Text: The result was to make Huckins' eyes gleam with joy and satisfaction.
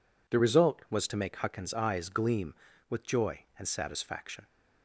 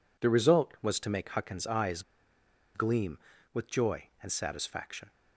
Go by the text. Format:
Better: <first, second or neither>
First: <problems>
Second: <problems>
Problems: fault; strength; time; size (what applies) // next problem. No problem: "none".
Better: first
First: none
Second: pauses between "eyes" and "gleam"; noticeable; at 2.0 s; 0.73 s long